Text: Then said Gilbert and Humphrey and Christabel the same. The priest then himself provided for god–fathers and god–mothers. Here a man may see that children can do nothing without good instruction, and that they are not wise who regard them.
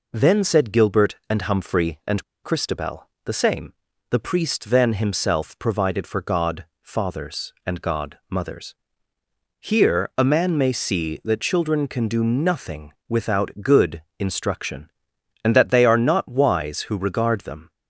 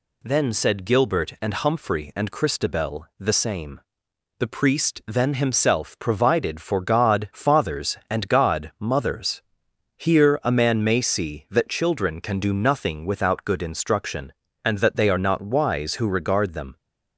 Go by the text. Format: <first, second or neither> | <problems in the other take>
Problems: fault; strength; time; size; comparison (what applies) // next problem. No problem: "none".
second | pauses between "and" and "Christabel"; slight; at 2.2 s; 0.21 s long // pauses between "Christabel" and "the"; slight; at 3.0 s; 0.20 s long // pauses between "nothing" and "without"; slight; at 12.9 s; 0.16 s long // pauses between "good" and "instruction"; slight; at 14.0 s; 0.18 s long